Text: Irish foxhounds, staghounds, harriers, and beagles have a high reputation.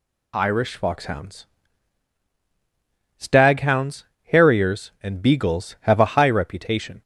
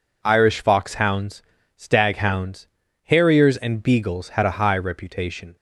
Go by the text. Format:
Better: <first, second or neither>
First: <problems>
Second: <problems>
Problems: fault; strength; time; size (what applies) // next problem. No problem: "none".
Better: first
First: none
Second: says "had" for "have"; at 4.3 s